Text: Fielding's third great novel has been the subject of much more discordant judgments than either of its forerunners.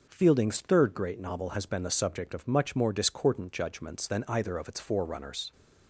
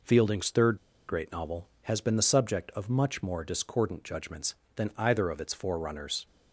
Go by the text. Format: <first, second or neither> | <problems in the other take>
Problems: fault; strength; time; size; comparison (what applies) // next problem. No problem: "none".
first | pauses between "third" and "great"; slight; at 0.7 s; 0.31 s long